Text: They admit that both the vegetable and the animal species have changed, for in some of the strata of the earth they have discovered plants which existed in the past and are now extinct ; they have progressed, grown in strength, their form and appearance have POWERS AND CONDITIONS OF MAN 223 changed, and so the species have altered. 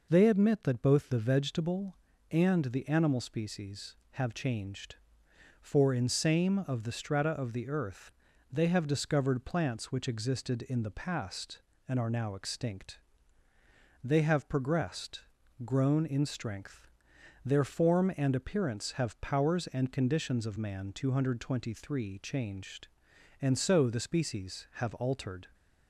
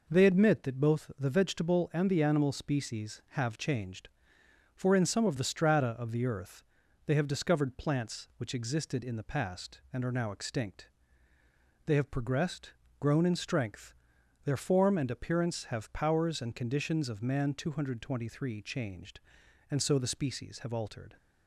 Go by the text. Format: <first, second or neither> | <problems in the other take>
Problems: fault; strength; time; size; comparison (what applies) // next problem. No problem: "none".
second | says "same" for "some"; at 6.0 s // pauses between "earth" and "they"; at 8.1 s; 0.40 s long; also in the second